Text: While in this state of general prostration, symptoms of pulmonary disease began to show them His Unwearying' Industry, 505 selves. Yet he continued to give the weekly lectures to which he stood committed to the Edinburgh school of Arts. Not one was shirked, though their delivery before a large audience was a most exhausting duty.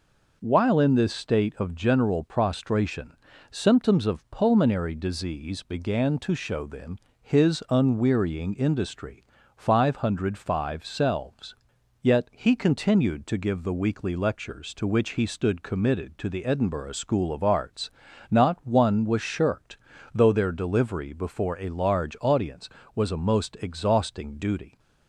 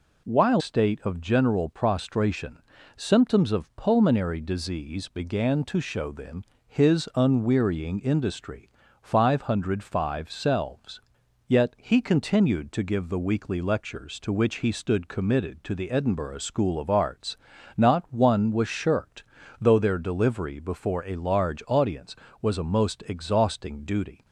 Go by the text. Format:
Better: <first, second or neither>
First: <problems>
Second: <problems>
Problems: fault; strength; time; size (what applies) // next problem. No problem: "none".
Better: first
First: pauses between "them" and "His"; slight; at 6.9 s; 0.24 s long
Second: skips "in this"; at 0.6 s // pauses between "them" and "His"; slight; at 6.4 s; 0.24 s long